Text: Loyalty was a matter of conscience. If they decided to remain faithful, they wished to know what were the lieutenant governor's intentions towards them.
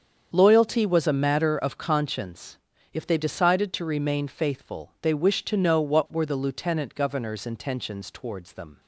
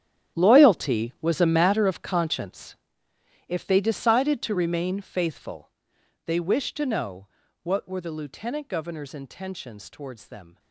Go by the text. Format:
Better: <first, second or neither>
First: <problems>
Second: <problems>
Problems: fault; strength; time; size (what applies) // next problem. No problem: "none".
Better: first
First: starts louder than the rest; strong; until 1.3 s; 7.5 dB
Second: gets quieter; strong; throughout; 16.5 dB // starts louder than the rest; strong; until 1.4 s; 10.5 dB // pauses between "know" and "what"; slight; at 7.2 s; 0.36 s long